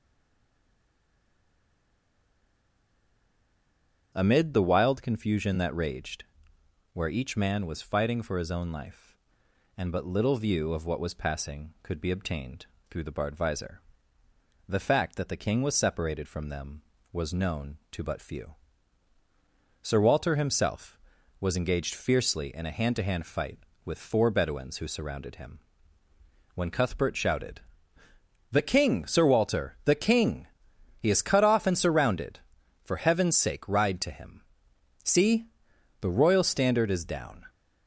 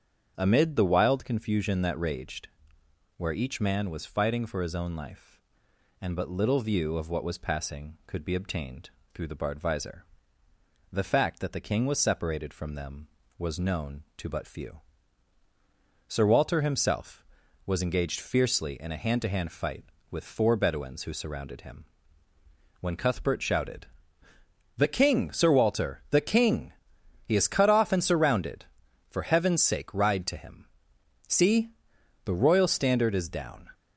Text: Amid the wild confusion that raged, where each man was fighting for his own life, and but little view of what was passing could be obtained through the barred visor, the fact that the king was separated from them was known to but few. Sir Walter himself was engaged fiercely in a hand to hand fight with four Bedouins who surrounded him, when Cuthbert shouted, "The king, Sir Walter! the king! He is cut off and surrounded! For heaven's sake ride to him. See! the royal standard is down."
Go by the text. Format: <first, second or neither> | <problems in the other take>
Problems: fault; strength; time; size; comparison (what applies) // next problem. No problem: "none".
second | stays silent before the first word; strong; until 4.1 s; 4.1 s long // starts louder than the rest; strong; until 5.1 s; 8 dB; strong in the second // pauses between "obtained" and "through"; slight; at 12.6 s; 0.24 s long; slight in the second